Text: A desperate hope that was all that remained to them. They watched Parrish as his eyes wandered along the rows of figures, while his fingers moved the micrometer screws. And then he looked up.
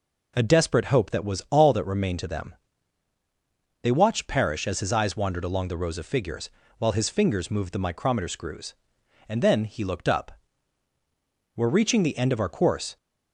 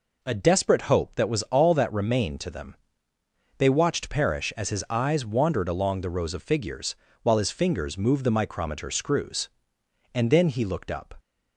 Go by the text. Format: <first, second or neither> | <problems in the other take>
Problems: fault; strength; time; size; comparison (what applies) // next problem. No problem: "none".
second | goes on to say "We're reaching the end of our course"; from 11.5 s on; 1.4 s long